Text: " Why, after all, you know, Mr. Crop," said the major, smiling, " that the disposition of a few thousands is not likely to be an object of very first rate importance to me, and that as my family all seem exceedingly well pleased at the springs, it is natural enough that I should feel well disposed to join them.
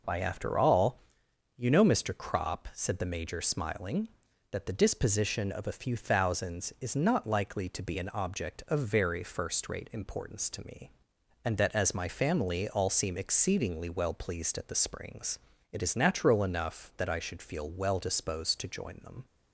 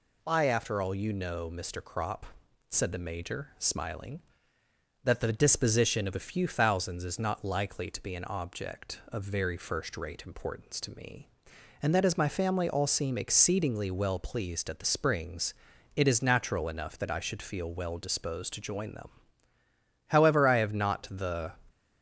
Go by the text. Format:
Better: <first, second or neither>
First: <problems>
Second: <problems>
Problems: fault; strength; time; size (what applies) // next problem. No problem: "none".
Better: first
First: none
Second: goes on to say "However I have not the"; from 20.0 s on; 1.4 s long